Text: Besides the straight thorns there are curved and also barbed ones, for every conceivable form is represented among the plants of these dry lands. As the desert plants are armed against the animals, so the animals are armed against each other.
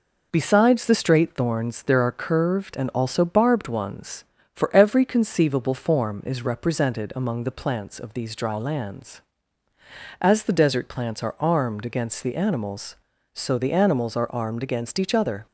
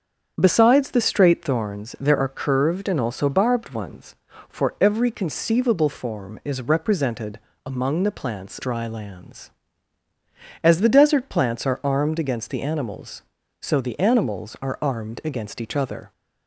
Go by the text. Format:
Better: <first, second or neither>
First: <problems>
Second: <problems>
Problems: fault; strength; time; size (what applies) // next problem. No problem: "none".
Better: first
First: none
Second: starts louder than the rest; strong; until 1.3 s; 7.5 dB // pauses between "represented" and "among"; slight; at 7.3 s; 0.24 s long // skips "of these"; at 8.5 s